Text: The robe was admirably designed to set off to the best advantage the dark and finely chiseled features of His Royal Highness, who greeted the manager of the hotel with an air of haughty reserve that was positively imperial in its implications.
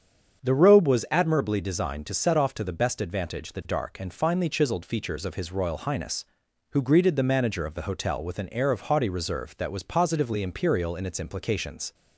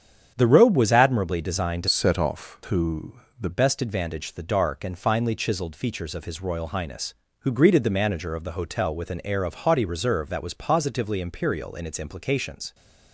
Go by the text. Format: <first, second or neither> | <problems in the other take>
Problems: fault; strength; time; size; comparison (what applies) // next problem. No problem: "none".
first | starts louder than the rest; strong; until 1.3 s; 8.5 dB; strong in the first // changes voice from "set" to "the"; from 1.8 to 3.5 s; 1.7 s long // pauses between "to" and "the"; slight; at 3.1 s; 0.26 s long